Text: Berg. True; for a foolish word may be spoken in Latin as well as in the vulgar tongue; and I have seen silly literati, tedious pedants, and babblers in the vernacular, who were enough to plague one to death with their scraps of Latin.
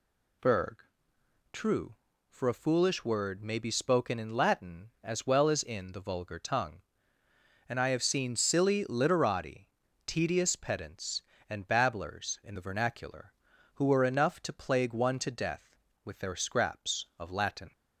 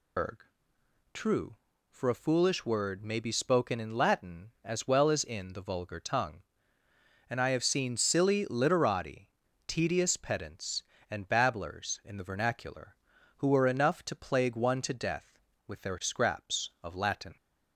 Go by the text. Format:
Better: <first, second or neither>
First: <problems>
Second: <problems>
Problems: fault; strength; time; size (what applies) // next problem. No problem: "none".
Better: first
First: none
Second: loses the start of "Berg"; at 0.1 s; 145 ms